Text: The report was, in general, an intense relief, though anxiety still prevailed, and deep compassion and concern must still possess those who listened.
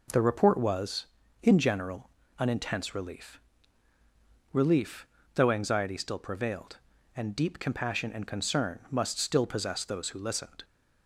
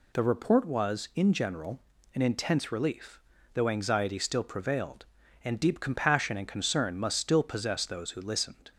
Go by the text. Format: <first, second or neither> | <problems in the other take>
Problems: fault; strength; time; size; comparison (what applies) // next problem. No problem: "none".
second | says "relief" twice; at 4.5 s